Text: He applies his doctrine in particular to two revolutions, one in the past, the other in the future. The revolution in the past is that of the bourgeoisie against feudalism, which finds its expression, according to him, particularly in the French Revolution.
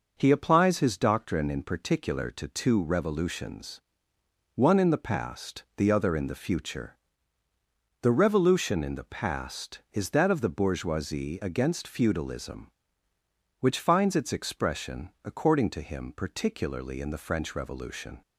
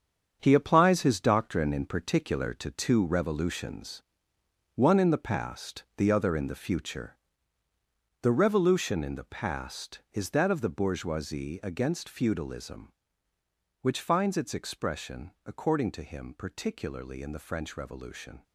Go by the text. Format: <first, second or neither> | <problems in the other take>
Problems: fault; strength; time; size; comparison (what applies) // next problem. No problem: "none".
first | gets quieter; strong; throughout; 8.5 dB